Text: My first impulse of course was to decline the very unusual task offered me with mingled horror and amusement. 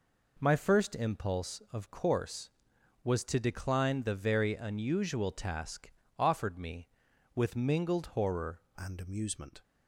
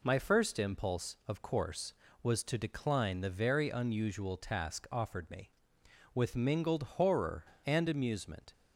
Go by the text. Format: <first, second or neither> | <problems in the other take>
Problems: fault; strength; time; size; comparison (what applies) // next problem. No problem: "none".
second | pauses between "task" and "offered"; slight; at 5.8 s; 0.28 s long // changes voice at "and"; from 8.7 s on; 0.9 s long